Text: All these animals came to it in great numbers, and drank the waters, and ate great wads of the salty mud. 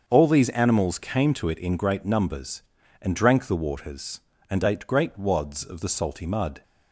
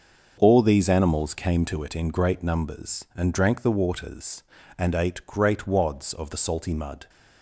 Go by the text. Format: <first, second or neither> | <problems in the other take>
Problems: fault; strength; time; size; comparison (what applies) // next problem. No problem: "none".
neither | starts louder than the rest; the same in both